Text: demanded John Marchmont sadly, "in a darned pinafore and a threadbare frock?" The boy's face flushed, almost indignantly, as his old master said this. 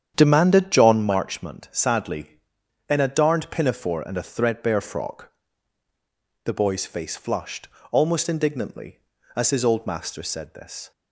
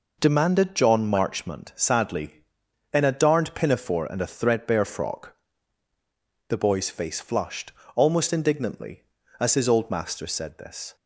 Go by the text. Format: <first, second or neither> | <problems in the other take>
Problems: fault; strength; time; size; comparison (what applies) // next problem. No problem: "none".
second | starts louder than the rest; strong; until 1.1 s; 8.5 dB